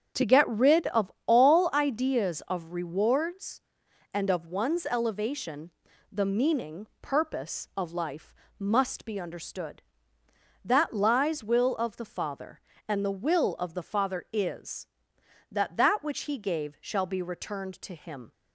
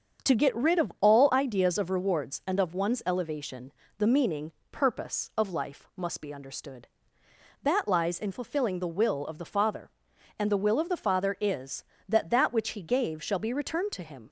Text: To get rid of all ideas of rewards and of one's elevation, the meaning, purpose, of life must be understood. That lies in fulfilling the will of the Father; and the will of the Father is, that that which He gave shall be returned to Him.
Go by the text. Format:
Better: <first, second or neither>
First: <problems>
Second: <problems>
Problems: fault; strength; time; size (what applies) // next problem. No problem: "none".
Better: second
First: starts louder than the rest; strong; until 1.3 s; 8 dB // pauses between "of" and "all"; slight; at 1.1 s; 0.16 s long // pauses between "life" and "must"; slight; at 8.3 s; 0.26 s long // skips "in fulfilling the"; at 11.4 s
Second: starts louder than the rest; until 1.3 s; 7 dB